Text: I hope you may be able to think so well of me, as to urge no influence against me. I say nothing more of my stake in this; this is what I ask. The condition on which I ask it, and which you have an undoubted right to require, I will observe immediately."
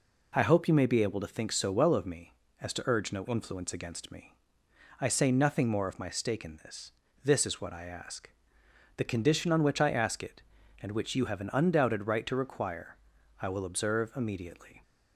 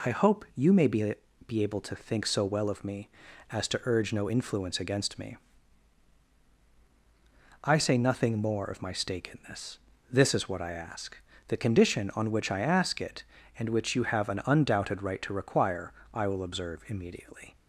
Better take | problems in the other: first | says "be" twice; at 1.4 s

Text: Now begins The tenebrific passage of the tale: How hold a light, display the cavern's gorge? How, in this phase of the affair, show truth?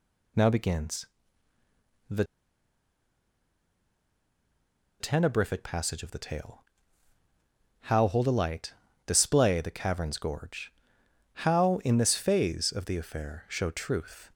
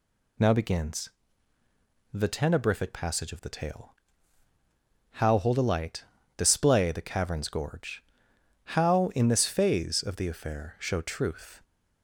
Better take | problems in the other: second | pauses between "begins" and "The"; at 1.0 s; 1.0 s long; also in the second // pauses between "The" and "tenebrific"; strong; at 2.2 s; 2.7 s long

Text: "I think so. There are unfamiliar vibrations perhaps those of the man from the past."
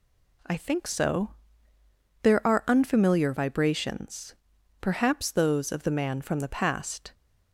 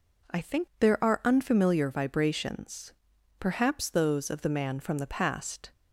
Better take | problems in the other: first | skips "so"; at 0.7 s // pauses between "vibrations" and "perhaps"; noticeable; at 2.9 s; 0.46 s long; noticeable in the first

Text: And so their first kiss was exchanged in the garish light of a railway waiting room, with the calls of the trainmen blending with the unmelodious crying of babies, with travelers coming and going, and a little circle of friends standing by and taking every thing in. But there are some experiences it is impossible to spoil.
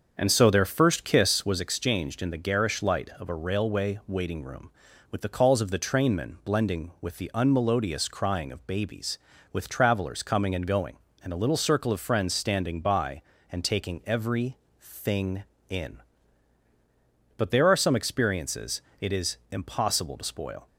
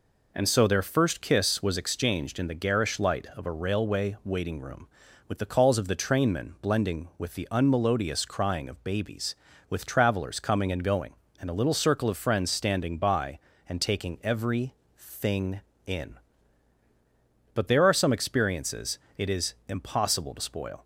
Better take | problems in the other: second | starts louder than the rest; until 1.5 s; 7 dB // pauses between "every" and "thing"; slight; at 14.5 s; 0.24 s long; slight in the second // pauses between "experiences" and "it"; slight; at 18.8 s; 0.18 s long; slight in the second

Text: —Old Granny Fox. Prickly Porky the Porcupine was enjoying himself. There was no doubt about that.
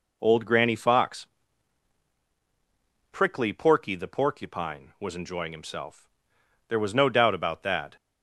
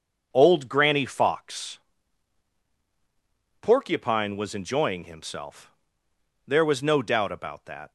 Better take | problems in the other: first | starts louder than the rest; until 1.3 s; 6.5 dB // skips "Prickly Porky the"; at 2.6 s

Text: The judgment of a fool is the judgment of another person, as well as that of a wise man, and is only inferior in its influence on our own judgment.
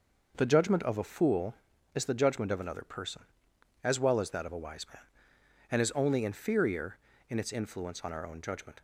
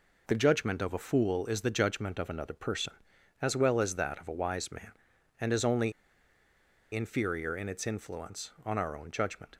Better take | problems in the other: first | pauses between "only" and "inferior"; at 5.9 s; 1.0 s long

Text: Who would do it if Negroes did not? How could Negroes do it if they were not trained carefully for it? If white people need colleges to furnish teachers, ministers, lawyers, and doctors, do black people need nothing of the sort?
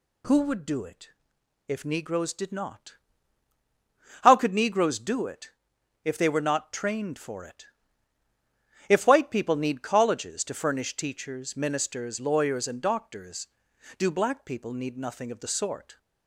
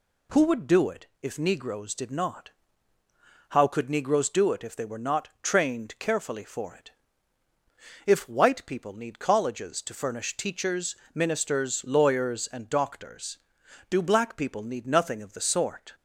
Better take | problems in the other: second | pauses between "it" and "if"; noticeable; at 1.0 s; 0.58 s long; slight in the second // pauses between "it" and "if"; noticeable; at 5.5 s; 0.52 s long // skips "carefully"; at 7.1 s

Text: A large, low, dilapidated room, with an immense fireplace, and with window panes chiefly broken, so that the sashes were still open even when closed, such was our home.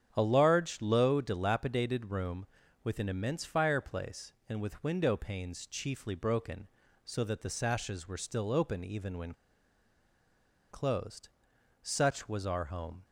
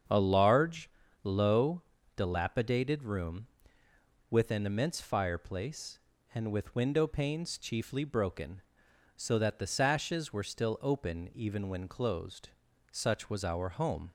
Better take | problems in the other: second | starts louder than the rest; strong; until 1.1 s; 8.5 dB; strong in the second // pauses between "when" and "closed"; strong; at 9.3 s; 1.3 s long

